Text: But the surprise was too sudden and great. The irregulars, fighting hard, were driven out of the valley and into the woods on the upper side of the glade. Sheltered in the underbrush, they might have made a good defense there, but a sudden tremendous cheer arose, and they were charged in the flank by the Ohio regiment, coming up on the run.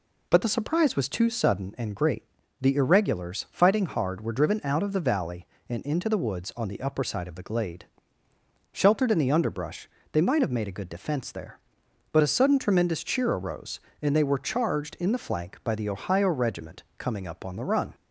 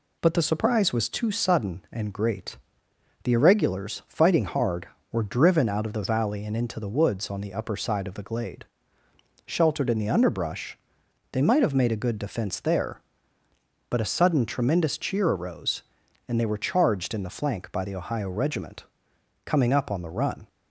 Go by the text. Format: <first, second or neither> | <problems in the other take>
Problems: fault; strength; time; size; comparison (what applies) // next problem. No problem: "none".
neither | none